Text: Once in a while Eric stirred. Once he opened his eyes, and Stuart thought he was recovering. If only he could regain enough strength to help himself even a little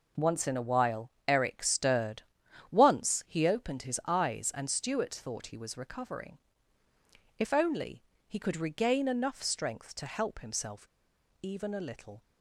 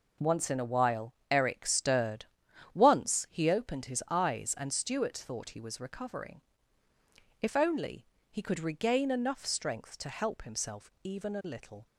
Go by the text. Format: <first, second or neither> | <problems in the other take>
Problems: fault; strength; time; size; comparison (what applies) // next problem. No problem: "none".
second | pauses between "while" and "Eric"; slight; at 1.1 s; 0.18 s long; slight in the second // pauses between "only" and "he"; slight; at 8.0 s; 0.24 s long; slight in the second // pauses between "himself" and "even"; noticeable; at 10.8 s; 0.54 s long